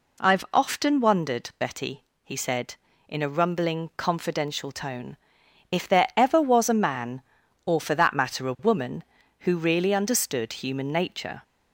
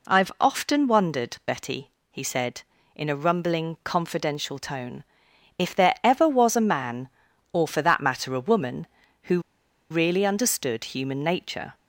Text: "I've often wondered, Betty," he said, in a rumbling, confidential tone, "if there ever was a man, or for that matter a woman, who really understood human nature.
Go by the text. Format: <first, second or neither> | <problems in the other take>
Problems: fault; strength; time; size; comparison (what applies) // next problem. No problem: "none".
first | pauses between "who" and "really"; noticeable; at 9.3 s; 0.50 s long